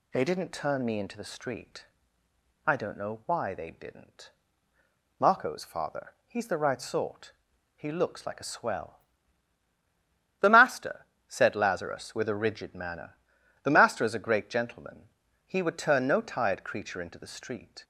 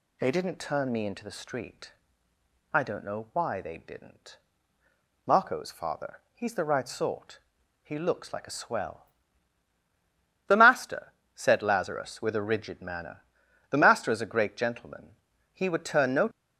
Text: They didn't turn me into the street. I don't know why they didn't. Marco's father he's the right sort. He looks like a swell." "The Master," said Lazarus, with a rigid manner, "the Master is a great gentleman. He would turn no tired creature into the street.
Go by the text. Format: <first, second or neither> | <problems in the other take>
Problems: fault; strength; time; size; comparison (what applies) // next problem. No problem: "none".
first | stops before "tired creature into the street"; at 16.3 s